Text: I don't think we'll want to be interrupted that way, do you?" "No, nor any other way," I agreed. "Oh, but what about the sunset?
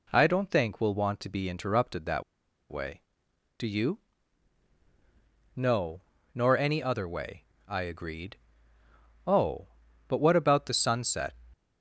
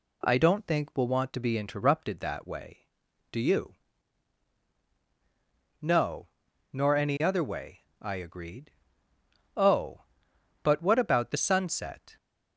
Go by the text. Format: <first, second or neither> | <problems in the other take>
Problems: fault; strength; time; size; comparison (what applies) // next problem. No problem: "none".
second | pauses between "that" and "way"; noticeable; at 2.2 s; 0.47 s long